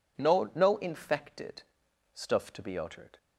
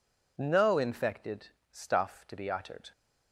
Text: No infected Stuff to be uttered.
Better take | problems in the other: second | says "No" twice; at 0.5 s // pauses between "infected" and "Stuff"; noticeable; at 1.6 s; 0.50 s long; slight in the second

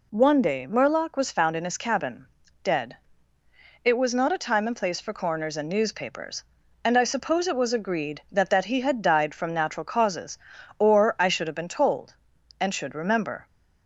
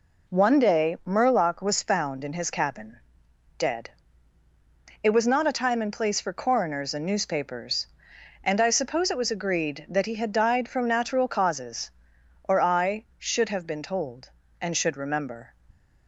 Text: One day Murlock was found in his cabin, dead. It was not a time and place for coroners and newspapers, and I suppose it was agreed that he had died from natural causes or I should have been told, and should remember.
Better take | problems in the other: second | says "that" twice; at 8.4 s

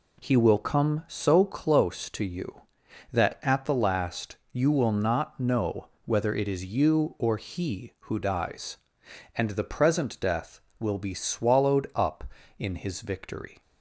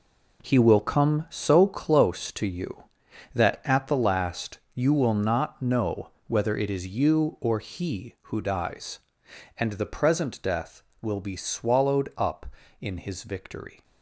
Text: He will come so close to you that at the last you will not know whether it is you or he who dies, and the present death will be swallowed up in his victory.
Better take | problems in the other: first | gets quieter; strong; throughout; 9.5 dB // pauses between "know" and "whether"; slight; at 6.0 s; 0.18 s long; slight in the first

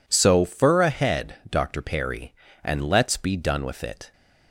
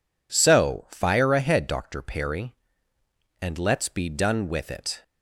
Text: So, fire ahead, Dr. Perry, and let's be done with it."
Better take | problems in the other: second | says "fur" for "fire"; at 0.4 s

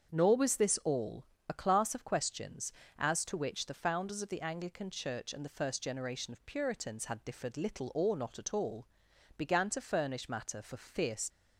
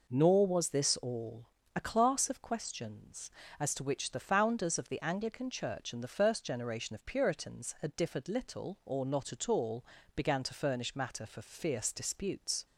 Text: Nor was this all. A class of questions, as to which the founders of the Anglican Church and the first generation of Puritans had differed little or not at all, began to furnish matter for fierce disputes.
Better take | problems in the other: second | starts louder than the rest; strong; until 1.1 s; 7 dB // stops before "disputes"; at 11.2 s

